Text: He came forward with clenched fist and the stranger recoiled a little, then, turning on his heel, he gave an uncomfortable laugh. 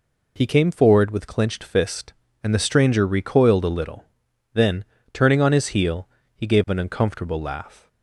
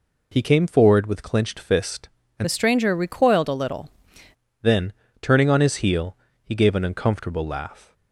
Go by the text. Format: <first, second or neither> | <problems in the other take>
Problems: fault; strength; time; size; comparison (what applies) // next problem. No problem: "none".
first | changes voice from "the" to "little"; from 2.4 to 3.8 s; 1.4 s long